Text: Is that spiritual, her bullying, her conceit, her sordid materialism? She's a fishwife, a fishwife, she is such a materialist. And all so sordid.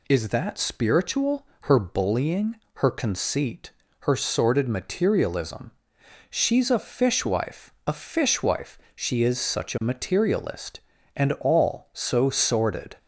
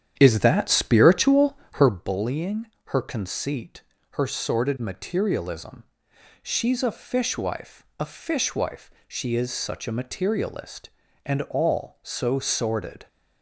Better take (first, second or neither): first